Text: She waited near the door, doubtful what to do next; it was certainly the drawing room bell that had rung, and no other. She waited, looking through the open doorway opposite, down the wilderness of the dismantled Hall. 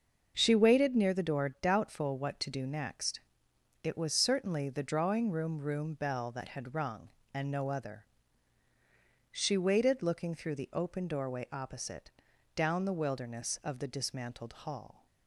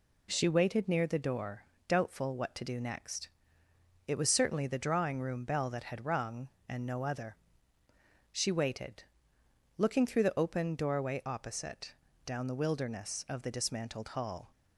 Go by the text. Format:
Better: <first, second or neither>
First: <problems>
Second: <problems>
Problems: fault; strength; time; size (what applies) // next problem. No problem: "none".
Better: second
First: starts louder than the rest; until 1.3 s; 6 dB // says "room" twice; at 5.5 s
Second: none